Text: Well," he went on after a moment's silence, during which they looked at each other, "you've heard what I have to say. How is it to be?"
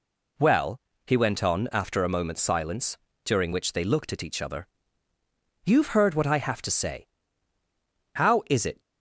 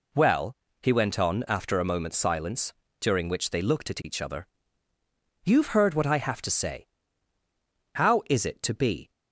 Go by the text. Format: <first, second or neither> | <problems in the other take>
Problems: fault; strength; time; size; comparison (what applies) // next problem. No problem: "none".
second | stops before "to be"; at 8.8 s